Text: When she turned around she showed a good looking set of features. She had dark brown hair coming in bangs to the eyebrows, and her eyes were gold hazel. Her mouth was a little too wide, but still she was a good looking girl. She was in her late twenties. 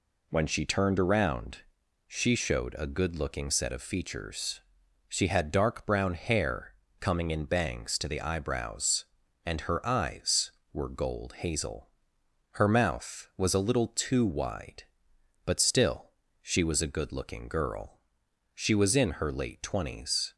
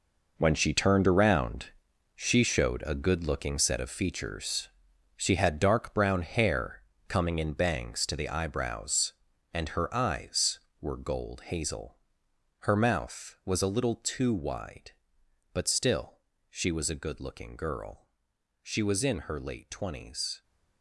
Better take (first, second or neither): first